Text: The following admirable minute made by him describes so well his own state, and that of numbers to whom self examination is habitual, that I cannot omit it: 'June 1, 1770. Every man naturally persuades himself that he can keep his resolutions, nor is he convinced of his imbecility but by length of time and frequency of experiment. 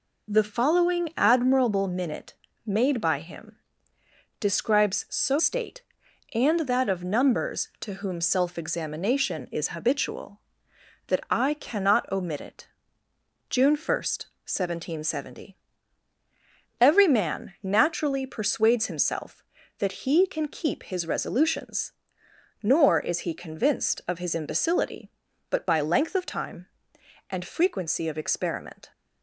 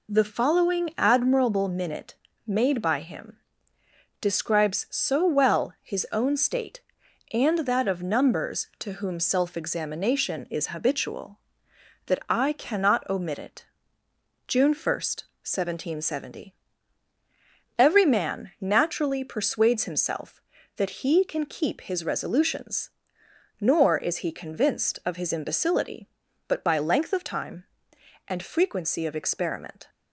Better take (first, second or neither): second